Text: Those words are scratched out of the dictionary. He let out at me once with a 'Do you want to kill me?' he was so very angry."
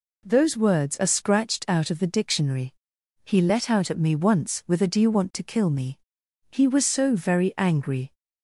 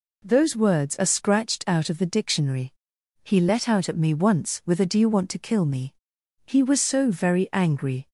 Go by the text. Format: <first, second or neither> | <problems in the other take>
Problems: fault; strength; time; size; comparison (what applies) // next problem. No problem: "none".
neither | none